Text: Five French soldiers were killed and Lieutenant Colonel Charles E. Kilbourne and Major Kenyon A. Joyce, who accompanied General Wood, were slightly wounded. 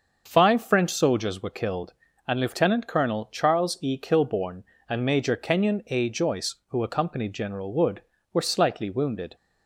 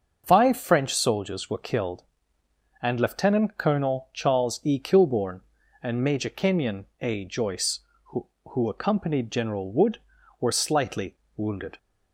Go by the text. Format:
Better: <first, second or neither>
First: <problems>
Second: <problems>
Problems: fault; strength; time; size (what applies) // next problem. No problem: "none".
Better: first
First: starts louder than the rest; until 1.2 s; 6.5 dB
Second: starts louder than the rest; until 1.2 s; 6.5 dB // says "who" twice; at 8.4 s // pauses between "slightly" and "wounded"; slight; at 11.1 s; 0.20 s long